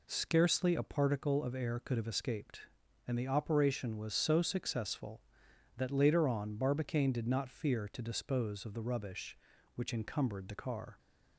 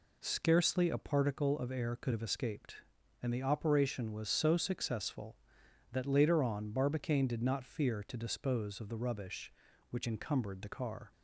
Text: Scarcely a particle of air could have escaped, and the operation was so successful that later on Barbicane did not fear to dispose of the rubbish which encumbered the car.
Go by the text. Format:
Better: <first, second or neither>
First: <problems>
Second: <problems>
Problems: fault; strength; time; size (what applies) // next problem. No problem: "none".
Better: neither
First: none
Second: none